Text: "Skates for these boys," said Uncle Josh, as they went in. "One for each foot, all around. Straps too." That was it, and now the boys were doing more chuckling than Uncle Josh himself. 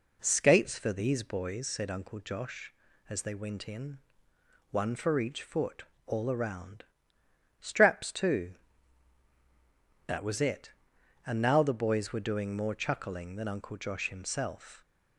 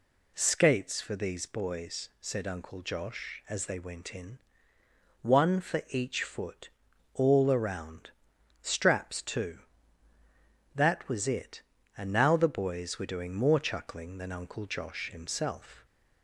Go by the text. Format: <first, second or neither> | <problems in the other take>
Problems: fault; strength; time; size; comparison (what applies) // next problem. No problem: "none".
neither | none